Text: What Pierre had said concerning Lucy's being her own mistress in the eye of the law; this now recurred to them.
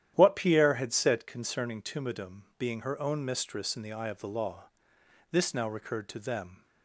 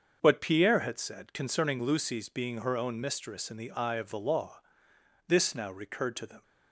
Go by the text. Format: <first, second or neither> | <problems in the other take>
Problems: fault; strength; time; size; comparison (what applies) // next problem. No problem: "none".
second | starts louder than the rest; strong; until 1.1 s; 11 dB; also in the second // says "Tumidum" for "Lucy's"; at 1.8 s